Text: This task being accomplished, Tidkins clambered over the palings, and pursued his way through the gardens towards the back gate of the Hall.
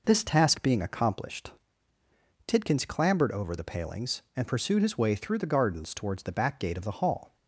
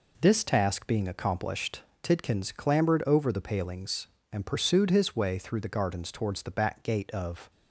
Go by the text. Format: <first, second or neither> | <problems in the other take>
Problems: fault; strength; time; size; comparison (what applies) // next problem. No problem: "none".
first | stops before "the Hall"; at 7.4 s